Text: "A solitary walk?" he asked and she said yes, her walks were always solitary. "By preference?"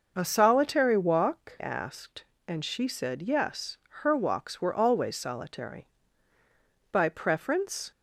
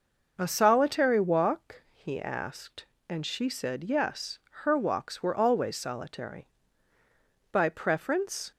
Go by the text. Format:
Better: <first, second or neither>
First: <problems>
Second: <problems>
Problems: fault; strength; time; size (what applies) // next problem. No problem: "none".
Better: second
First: skips "he"; at 1.5 s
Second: none